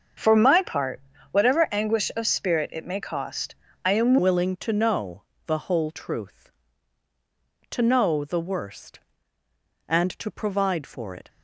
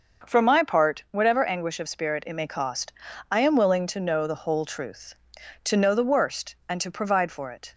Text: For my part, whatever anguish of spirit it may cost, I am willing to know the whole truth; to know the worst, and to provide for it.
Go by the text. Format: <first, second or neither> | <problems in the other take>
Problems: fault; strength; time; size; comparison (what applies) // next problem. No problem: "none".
second | starts louder than the rest; until 1.5 s; 6.5 dB; noticeable in the second // changes voice at "willing"; from 4.1 s on; 7.1 s long // pauses between "know" and "the"; slight; at 5.2 s; 0.22 s long